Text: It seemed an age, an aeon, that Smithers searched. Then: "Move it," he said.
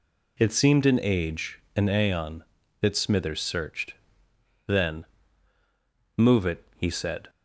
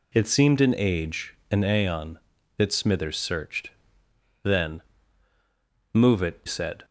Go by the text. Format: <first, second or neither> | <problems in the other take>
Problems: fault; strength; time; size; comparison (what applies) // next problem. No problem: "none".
first | skips "he"; at 6.4 s